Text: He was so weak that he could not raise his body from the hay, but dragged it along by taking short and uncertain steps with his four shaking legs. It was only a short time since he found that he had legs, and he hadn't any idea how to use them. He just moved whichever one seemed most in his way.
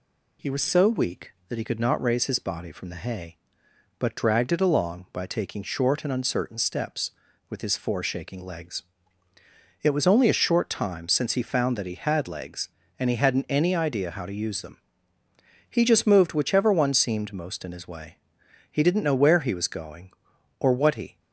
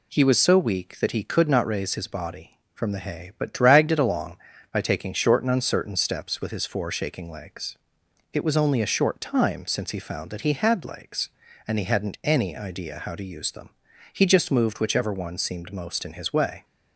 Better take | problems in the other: second | goes on to say "He didn't know where he was going or what he"; strong; from 18.7 s on; 2.4 s long

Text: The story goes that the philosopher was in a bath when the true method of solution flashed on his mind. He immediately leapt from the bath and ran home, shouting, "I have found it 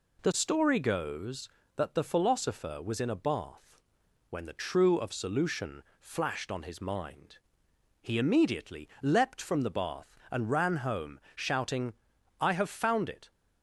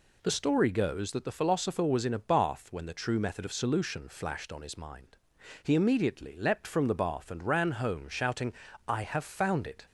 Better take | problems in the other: second | pauses between "bath" and "when"; noticeable; at 3.8 s; 0.48 s long // skips "method"; at 4.9 s // pauses between "solution" and "flashed"; slight; at 5.8 s; 0.18 s long

